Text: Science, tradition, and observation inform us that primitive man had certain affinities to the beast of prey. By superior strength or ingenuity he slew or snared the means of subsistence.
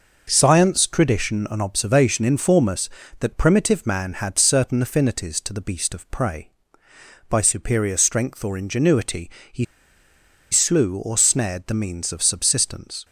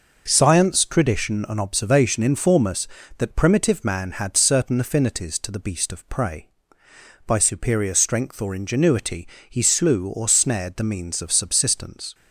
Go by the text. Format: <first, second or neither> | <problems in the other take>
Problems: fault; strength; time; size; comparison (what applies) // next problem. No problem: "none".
second | pauses between "ingenuity" and "he"; slight; at 9.3 s; 0.20 s long; slight in the second // pauses between "he" and "slew"; noticeable; at 9.6 s; 0.87 s long